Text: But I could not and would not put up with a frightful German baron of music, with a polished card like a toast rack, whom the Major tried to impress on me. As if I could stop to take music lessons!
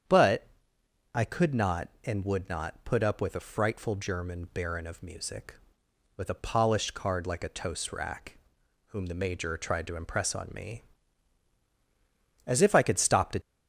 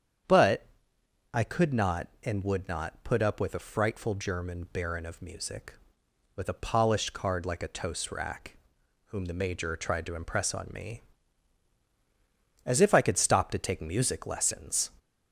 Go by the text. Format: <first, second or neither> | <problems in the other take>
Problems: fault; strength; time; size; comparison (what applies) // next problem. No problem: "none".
second | starts louder than the rest; strong; until 1.7 s; 8.5 dB; strong in the second // pauses between "But" and "I"; noticeable; at 0.4 s; 0.68 s long; noticeable in the second // stops before "take music lessons"; at 13.4 s